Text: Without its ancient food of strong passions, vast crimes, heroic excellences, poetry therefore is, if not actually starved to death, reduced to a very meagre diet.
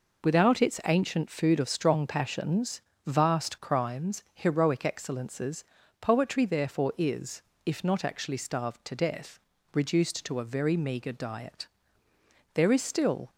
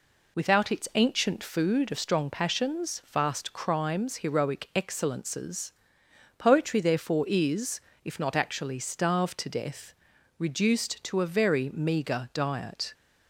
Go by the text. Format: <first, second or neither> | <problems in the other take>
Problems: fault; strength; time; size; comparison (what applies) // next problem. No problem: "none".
second | goes on to say "There is still"; noticeable; from 12.5 s on; 0.76 s long